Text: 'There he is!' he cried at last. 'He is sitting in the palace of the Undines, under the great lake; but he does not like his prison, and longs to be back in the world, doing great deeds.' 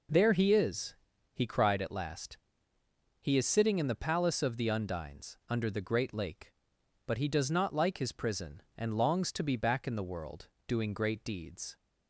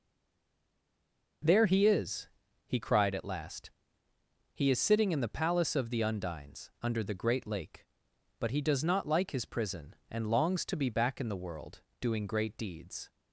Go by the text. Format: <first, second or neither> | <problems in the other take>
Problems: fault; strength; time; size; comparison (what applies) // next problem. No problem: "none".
first | stays silent before the first word; noticeable; until 1.4 s; 1.4 s long